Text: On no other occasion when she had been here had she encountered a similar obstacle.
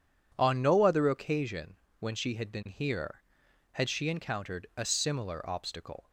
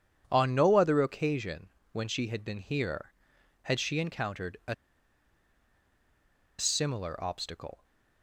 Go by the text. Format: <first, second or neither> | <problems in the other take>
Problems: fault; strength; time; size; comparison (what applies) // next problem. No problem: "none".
first | pauses between "occasion" and "when"; slight; at 1.6 s; 0.22 s long; slight in the first // pauses between "a" and "similar"; strong; at 4.7 s; 1.8 s long